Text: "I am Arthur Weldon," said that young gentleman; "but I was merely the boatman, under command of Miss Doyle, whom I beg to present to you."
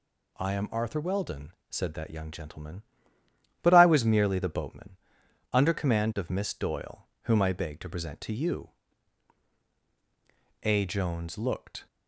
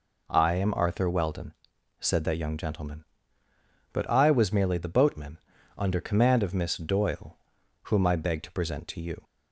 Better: second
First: goes on to say "A Jones looked"; noticeable; from 10.6 s on; 1.2 s long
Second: none

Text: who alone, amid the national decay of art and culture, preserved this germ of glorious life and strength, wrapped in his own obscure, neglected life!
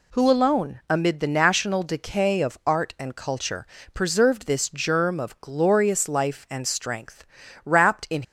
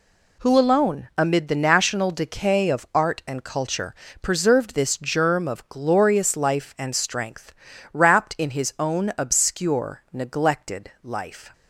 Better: second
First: stops before "his own obscure neglected life"; at 8.2 s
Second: none

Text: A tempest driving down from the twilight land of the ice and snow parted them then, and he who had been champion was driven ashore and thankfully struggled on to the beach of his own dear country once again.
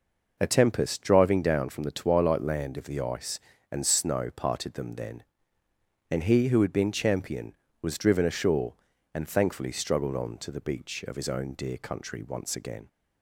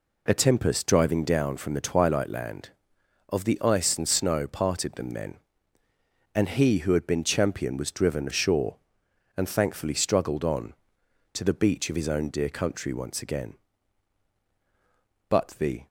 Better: first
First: none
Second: goes on to say "But the"; from 15.2 s on; 0.58 s long

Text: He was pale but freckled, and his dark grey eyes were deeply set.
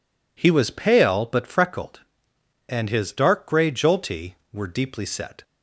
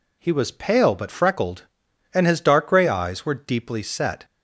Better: second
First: says "jolty" for "eyes"; at 3.7 s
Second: none

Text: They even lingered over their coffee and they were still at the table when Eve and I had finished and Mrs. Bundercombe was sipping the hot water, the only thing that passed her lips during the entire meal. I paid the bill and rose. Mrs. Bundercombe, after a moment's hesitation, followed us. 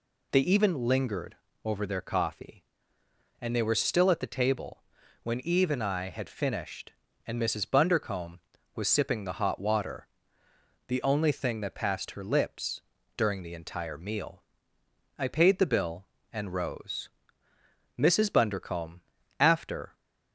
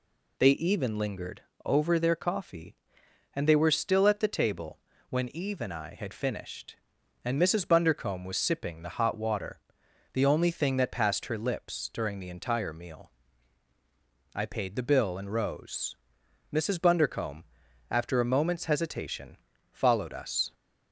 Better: second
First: pauses between "lingered" and "over"; slight; at 1.3 s; 0.28 s long // pauses between "table" and "when"; at 4.8 s; 0.40 s long // pauses between "lips" and "during"; slight; at 12.7 s; 0.36 s long // stops before "a moment's hesitation followed us"; at 19.9 s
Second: pauses between "lingered" and "over"; slight; at 1.4 s; 0.24 s long // pauses between "table" and "when"; slight; at 4.7 s; 0.30 s long

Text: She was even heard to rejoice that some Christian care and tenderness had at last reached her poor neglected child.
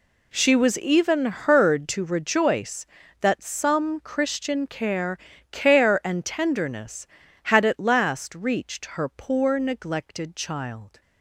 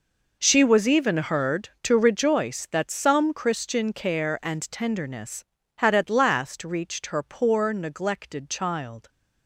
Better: second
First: says "care" twice; at 5.5 s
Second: none

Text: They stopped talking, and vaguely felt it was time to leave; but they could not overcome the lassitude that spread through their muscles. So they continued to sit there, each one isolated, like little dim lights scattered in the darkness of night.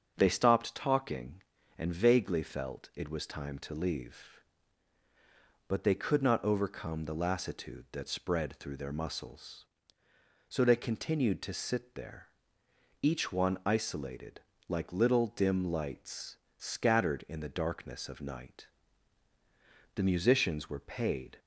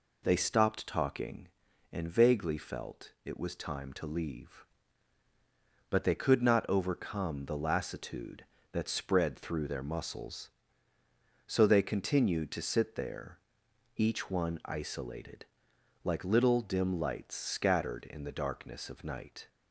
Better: second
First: starts louder than the rest; until 1.1 s; 7 dB // pauses between "lights" and "scattered"; slight; at 16.3 s; 0.22 s long // goes on to say "The musicians were paid"; from 19.9 s on; 1.4 s long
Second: none

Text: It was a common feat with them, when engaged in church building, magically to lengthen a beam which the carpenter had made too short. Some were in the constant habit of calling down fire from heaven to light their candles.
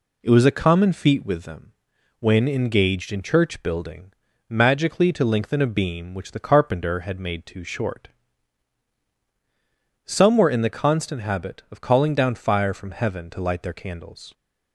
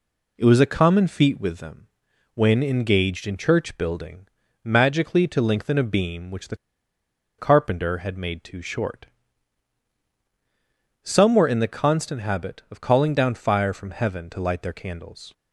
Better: first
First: none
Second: pauses between "the" and "carpenter"; noticeable; at 6.5 s; 0.82 s long

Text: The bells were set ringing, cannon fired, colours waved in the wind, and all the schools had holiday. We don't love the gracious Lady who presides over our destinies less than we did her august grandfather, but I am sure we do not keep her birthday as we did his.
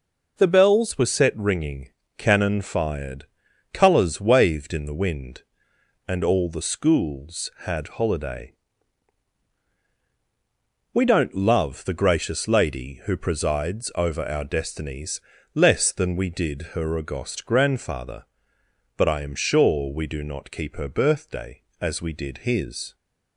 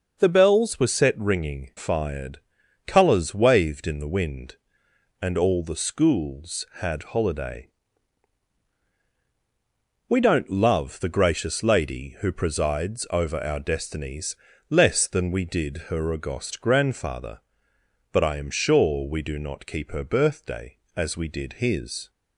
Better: first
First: pauses between "destinies" and "less"; slight; at 15.2 s; 0.34 s long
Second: skips "cannon"; at 1.7 s // pauses between "destinies" and "less"; slight; at 14.3 s; 0.34 s long

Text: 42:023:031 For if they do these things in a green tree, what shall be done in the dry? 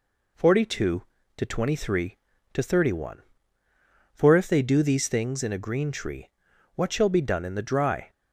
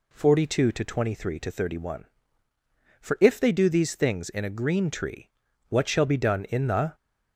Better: first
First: none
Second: stops before "dry"; at 6.9 s

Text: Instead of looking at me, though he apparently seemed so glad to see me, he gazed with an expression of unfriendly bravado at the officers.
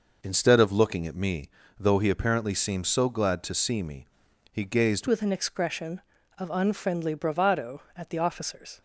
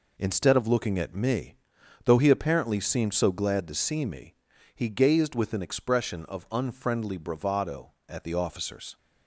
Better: second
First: changes voice at "with"; from 5.0 s on; 3.8 s long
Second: none

